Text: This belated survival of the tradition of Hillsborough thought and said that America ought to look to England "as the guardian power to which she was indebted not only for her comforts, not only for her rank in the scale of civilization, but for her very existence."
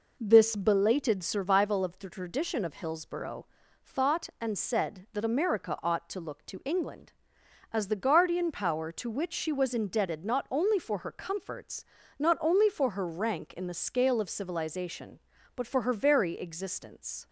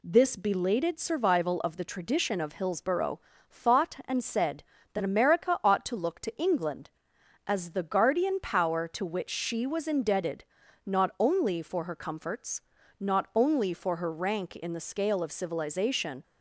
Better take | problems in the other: first | pauses between "Hillsborough" and "thought"; slight; at 3.1 s; 0.32 s long; also in the first // pauses between "indebted" and "not"; at 10.4 s; 0.42 s long // stops before "but for her very existence"; at 16.2 s

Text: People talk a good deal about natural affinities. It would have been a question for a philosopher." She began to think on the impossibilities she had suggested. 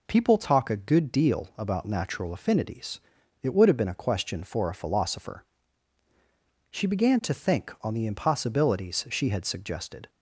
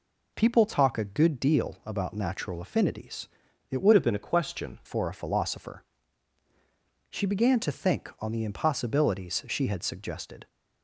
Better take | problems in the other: first | changes voice from "have" to "question"; from 3.9 to 4.7 s; 0.8 s long

